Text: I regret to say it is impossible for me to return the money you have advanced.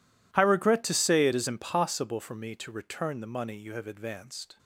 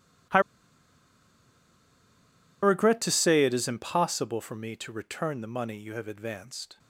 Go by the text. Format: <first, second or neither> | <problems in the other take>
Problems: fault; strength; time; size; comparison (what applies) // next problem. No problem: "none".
first | pauses between "I" and "regret"; strong; at 0.4 s; 2.2 s long